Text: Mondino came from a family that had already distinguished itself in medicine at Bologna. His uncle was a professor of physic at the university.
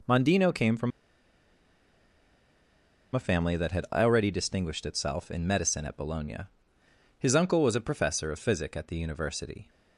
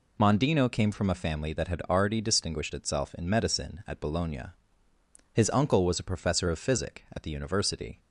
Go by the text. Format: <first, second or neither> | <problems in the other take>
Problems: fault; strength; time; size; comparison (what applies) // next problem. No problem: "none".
second | pauses between "from" and "a"; strong; at 0.9 s; 2.2 s long